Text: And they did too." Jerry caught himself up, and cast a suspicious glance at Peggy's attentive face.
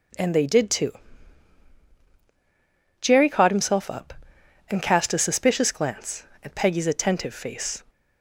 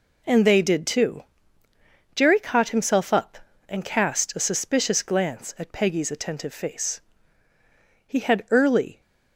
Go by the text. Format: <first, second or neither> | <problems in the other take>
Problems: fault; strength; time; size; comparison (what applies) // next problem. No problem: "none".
first | goes on to say "He had early"; noticeable; from 8.0 s on; 0.94 s long